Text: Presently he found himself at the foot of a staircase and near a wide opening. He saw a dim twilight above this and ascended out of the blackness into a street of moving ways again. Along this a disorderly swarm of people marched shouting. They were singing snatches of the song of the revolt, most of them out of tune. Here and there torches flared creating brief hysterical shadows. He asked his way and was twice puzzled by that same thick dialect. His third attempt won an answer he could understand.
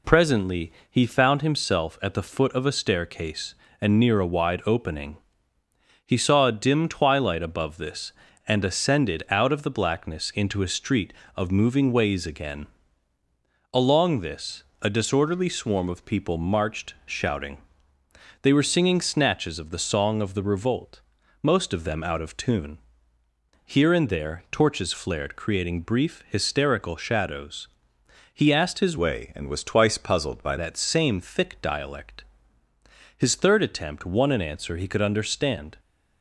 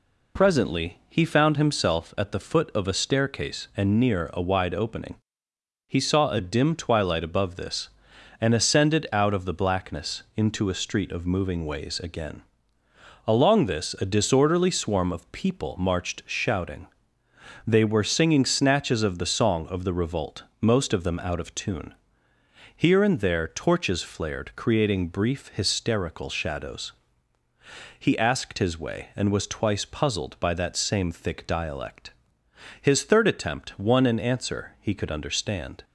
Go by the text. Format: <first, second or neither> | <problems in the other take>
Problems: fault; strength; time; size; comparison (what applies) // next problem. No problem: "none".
second | pauses between "Presently" and "he"; slight; at 0.7 s; 0.18 s long // pauses between "this" and "a"; slight; at 14.6 s; 0.22 s long // changes voice from "way" to "by"; from 28.9 to 30.5 s; 1.6 s long